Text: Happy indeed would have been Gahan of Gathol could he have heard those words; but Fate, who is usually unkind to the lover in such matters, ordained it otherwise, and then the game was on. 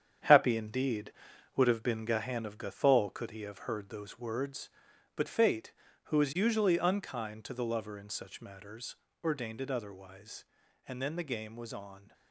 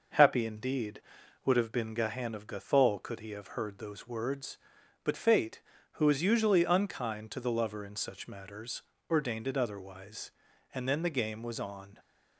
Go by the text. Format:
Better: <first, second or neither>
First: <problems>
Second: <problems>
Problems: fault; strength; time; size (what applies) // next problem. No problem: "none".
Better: second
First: gets quieter; strong; throughout; 7.5 dB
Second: none